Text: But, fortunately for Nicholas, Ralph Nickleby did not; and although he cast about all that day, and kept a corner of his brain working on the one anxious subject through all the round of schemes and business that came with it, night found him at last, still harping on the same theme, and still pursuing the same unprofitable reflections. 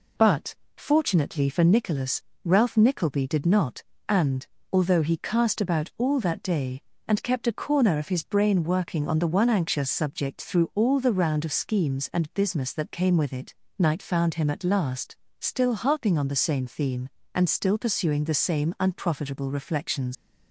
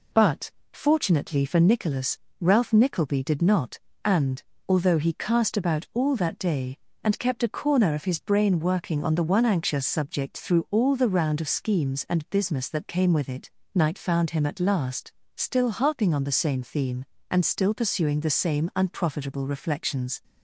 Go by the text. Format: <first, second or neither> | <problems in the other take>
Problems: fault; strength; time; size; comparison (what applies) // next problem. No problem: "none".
second | pauses between "and" and "although"; slight; at 4.4 s; 0.26 s long; slight in the second // leaves "reflections" unfinished; at 20.1 s; 120 ms